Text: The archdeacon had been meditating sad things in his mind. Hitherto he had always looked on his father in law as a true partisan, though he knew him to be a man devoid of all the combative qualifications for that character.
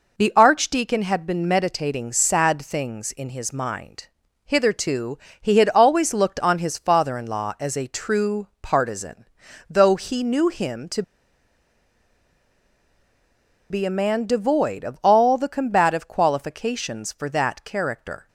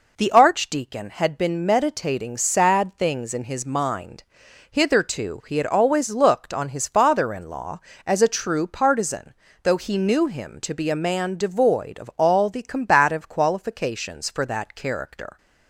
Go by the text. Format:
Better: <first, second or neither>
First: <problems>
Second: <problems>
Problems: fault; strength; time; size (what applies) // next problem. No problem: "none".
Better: second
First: pauses between "Hitherto" and "he"; slight; at 5.1 s; 0.24 s long // pauses between "to" and "be"; strong; at 11.0 s; 2.6 s long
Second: none